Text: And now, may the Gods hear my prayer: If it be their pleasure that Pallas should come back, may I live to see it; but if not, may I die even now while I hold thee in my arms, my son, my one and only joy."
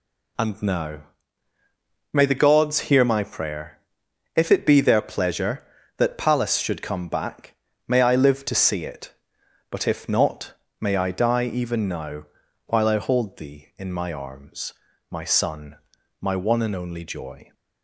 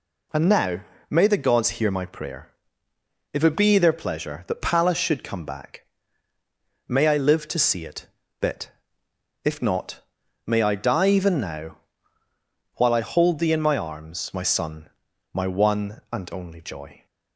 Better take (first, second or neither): first